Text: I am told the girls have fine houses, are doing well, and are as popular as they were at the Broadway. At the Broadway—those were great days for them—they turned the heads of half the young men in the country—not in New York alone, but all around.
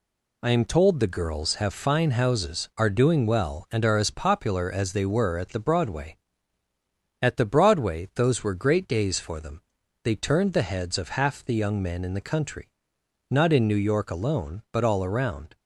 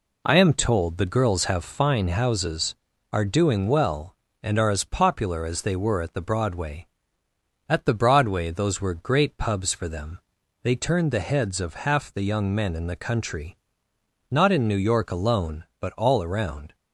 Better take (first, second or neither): first